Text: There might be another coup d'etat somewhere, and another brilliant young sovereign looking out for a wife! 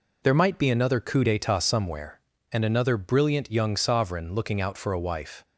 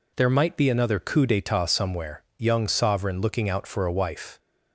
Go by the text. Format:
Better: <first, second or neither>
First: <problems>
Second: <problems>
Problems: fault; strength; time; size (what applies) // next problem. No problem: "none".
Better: first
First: none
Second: skips "and another brilliant"; at 2.3 s